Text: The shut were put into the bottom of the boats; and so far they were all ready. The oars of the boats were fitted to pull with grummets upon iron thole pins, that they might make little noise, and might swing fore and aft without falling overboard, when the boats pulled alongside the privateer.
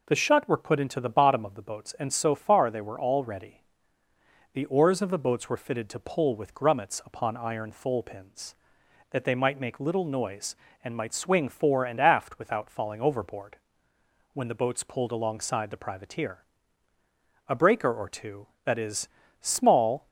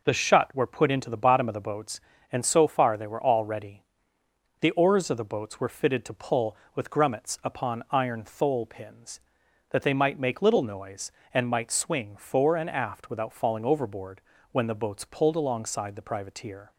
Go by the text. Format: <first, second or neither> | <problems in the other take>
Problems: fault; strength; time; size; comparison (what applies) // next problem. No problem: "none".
second | goes on to say "A breaker or two that is small"; strong; from 17.4 s on; 2.6 s long